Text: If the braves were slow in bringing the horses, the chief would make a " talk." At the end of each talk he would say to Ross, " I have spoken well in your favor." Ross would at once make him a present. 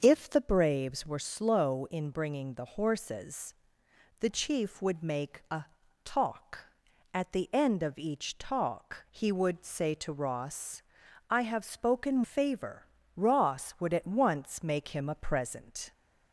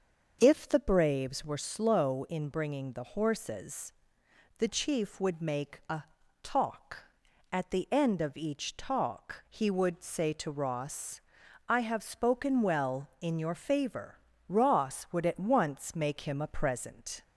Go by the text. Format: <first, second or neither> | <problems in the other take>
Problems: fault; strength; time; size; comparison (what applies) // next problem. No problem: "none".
second | starts louder than the rest; until 1.0 s; 6.5 dB; also in the second // skips "well in your"; at 12.2 s